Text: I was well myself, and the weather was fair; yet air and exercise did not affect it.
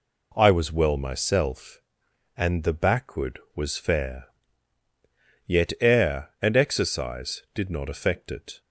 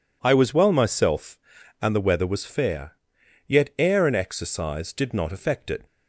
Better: second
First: says "backward" for "weather"; at 2.7 s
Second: none

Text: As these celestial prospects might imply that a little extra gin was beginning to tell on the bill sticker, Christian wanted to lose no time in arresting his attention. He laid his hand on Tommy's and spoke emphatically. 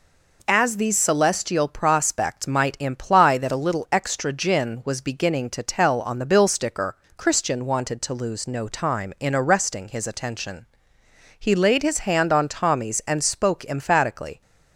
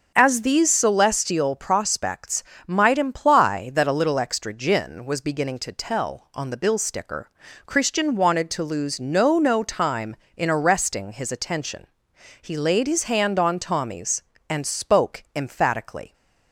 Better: first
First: none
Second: starts louder than the rest; until 1.1 s; 6.5 dB // pauses between "prospects" and "might"; slight; at 2.4 s; 0.24 s long // says "no" twice; at 9.3 s

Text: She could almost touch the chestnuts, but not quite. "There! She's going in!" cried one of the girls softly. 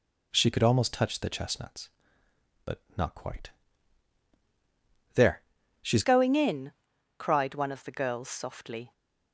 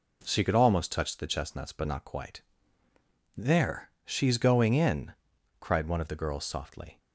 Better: second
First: pauses between "but" and "not"; slight; at 2.7 s; 0.16 s long // changes voice at "going"; from 6.0 s on; 2.9 s long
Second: none

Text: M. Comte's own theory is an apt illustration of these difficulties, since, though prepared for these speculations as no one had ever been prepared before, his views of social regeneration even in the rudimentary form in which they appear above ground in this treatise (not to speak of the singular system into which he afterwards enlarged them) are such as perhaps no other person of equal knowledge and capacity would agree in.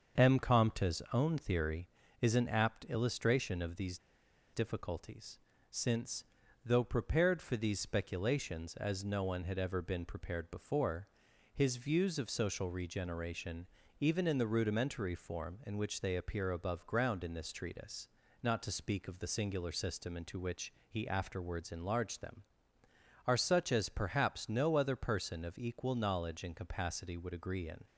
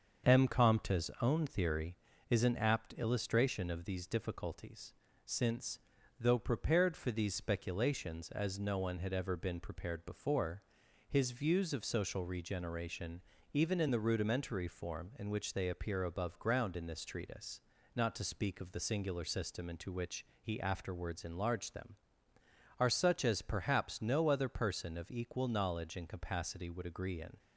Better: second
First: starts louder than the rest; until 1.2 s; 7 dB // pauses between "these" and "difficulties"; noticeable; at 3.9 s; 0.54 s long // pauses between "regeneration" and "even"; slight; at 13.6 s; 0.32 s long // pauses between "which" and "he"; slight; at 20.7 s; 0.16 s long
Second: starts louder than the rest; until 1.3 s; 7 dB // pauses between "regeneration" and "even"; slight; at 13.2 s; 0.30 s long // pauses between "which" and "he"; slight; at 20.2 s; 0.16 s long

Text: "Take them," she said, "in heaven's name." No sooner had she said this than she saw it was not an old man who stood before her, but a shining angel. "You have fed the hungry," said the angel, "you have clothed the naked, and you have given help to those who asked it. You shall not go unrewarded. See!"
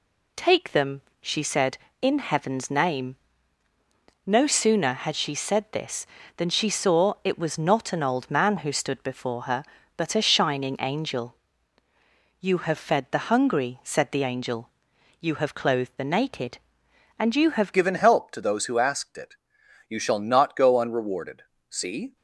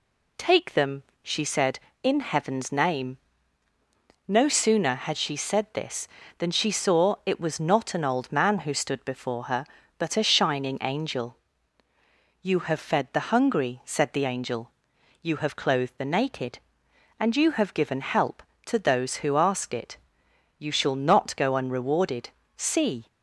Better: second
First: changes voice at "given"; from 17.7 s on; 4.4 s long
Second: none

